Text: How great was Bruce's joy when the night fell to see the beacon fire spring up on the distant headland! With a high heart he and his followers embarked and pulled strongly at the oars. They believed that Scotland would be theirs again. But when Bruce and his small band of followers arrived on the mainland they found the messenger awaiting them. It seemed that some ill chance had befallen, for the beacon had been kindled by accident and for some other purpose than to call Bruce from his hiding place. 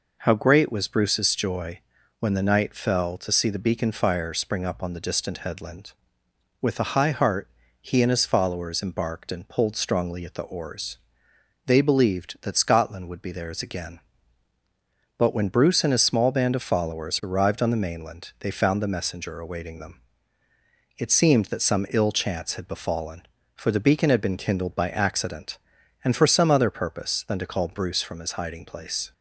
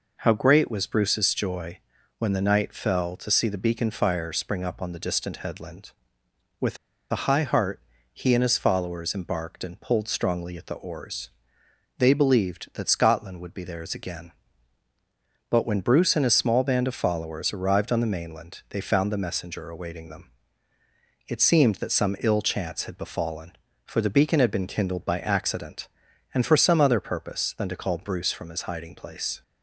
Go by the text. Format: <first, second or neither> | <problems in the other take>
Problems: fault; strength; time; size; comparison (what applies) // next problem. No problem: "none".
first | pauses between "joy" and "when"; at 1.7 s; 0.40 s long; also in the first // pauses between "With" and "a"; slight; at 6.7 s; 0.35 s long // pauses between "heart" and "he"; slight; at 7.8 s; 0.32 s long; slight in the first